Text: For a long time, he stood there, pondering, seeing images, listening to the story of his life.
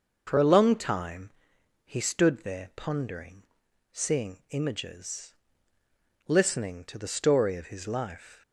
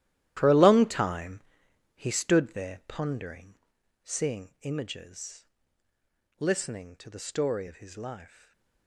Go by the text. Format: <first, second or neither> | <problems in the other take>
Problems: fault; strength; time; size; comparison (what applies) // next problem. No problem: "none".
first | gets quieter; strong; throughout; 13.5 dB // stays silent after the last word; slight; from 8.2 s on; 0.6 s long